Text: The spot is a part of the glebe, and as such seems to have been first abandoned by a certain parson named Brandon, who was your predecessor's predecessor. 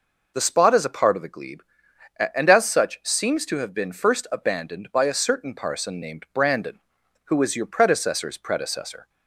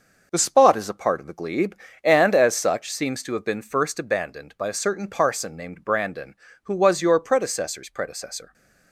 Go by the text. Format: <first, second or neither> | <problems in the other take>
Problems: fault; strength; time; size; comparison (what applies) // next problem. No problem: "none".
first | gets quieter; strong; throughout; 7 dB